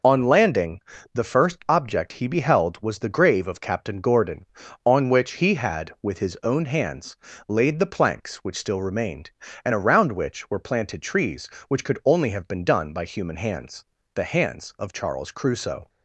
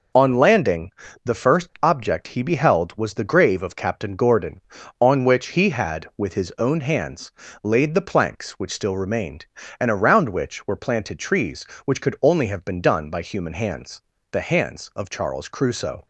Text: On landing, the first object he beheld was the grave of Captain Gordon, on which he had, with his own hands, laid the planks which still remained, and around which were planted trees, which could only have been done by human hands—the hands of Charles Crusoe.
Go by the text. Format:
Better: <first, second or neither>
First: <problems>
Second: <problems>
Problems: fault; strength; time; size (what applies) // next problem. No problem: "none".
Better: neither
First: none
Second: none